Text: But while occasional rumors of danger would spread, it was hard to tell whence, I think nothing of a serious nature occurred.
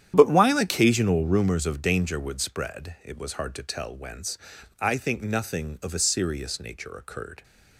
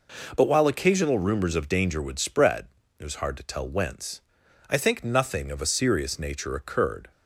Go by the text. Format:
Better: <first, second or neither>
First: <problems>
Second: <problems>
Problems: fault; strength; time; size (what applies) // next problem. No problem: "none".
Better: second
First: starts louder than the rest; strong; until 1.5 s; 10 dB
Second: none